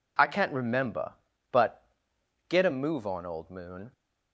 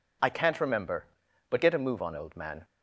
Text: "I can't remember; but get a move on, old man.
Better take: second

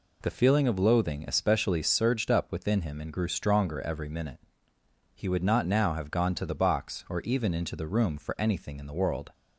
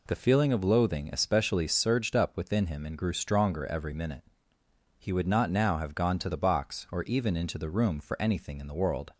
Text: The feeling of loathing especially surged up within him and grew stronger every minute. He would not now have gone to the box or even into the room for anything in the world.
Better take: neither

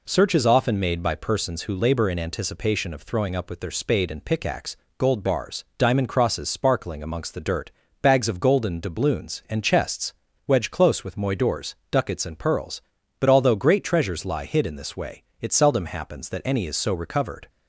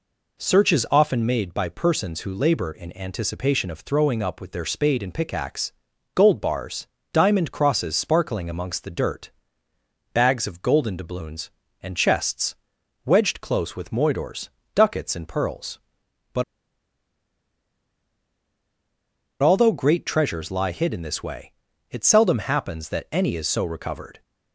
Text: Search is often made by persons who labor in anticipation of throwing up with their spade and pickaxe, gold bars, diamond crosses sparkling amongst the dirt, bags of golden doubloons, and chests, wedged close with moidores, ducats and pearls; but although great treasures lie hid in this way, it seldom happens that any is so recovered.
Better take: first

